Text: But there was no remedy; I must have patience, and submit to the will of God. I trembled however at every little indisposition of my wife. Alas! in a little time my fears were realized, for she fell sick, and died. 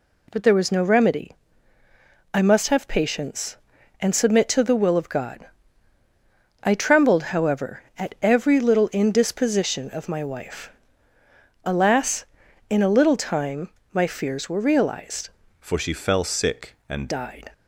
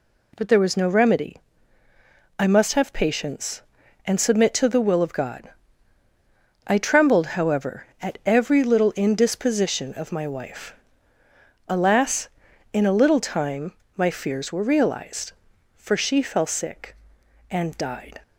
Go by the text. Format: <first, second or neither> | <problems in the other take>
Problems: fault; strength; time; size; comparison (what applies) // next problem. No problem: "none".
second | pauses between "time" and "my"; slight; at 13.6 s; 0.22 s long; slight in the second // changes voice from "for" to "and"; from 15.6 to 17.0 s; 1.4 s long